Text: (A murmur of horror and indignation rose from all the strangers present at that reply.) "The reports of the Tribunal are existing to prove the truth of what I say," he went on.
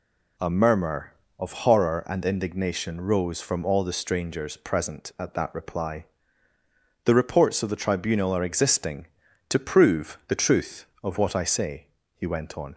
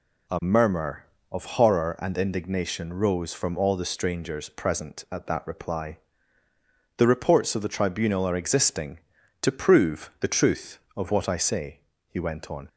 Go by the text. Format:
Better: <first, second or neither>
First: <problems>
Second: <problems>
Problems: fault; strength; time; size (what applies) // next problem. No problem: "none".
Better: neither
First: none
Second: none